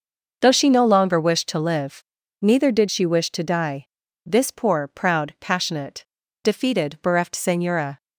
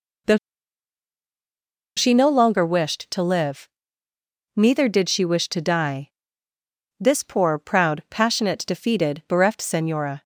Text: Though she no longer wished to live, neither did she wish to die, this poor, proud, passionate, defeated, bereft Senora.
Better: first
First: none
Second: pauses between "Though" and "she"; strong; at 0.3 s; 1.5 s long

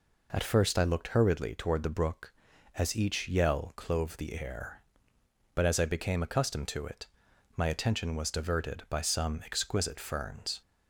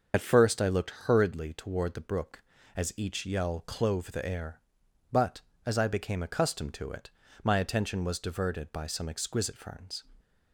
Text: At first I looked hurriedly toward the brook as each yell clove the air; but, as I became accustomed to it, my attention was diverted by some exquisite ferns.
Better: first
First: none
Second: loses the start of "At"; at 0.1 s; 45 ms // starts louder than the rest; noticeable; until 1.1 s; 6 dB

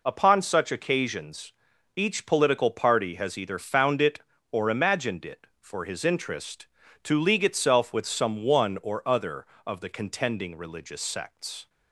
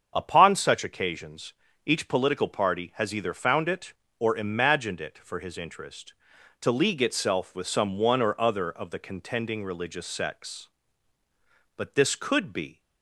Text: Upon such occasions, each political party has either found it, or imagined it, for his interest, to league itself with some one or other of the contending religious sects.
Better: first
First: none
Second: starts louder than the rest; until 1.1 s; 7 dB // goes on to say "But this could be"; noticeable; from 11.7 s on; 1.0 s long

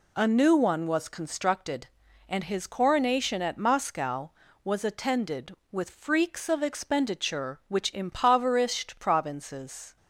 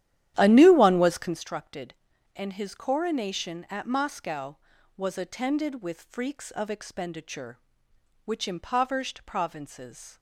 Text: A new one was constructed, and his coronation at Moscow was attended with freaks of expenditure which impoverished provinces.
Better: first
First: none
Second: starts louder than the rest; strong; until 1.4 s; 11.5 dB

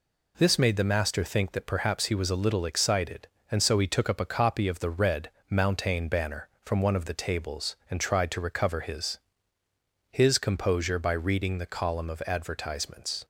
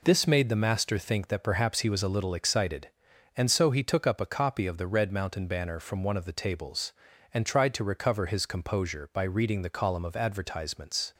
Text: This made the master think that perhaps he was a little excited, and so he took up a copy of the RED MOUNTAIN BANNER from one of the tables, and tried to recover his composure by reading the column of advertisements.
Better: second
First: pauses between "RED" and "MOUNTAIN"; slight; at 5.2 s; 0.20 s long // says "his" twice; at 10.1 s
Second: none

